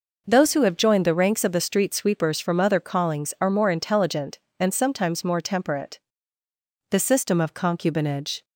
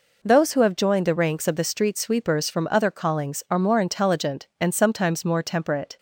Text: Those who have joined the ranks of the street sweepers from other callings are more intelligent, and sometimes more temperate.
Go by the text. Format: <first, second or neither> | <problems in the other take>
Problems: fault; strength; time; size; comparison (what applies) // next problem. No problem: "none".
second | goes on to say "The system of concubinage"; from 6.8 s on; 1.5 s long